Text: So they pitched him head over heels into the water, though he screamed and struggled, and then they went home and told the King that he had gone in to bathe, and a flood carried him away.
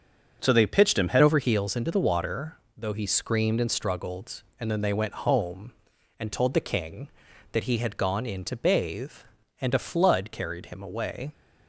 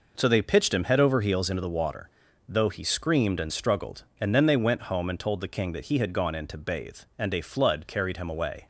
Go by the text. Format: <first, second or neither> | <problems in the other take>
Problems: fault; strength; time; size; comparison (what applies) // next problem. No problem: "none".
second | changes voice at "over"; from 1.2 s on; 10.1 s long